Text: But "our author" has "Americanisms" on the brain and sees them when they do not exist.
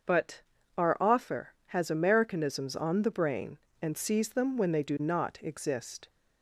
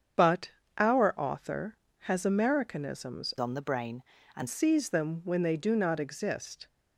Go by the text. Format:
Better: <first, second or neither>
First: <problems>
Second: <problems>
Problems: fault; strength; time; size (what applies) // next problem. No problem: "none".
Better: first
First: starts louder than the rest; until 1.4 s; 6.5 dB // pauses between "But" and "our"; slight; at 0.4 s; 0.34 s long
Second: starts louder than the rest; strong; until 1.4 s; 7.5 dB // pauses between "But" and "our"; slight; at 0.5 s; 0.26 s long // changes voice from "on" to "and"; from 3.3 to 4.4 s; 1.1 s long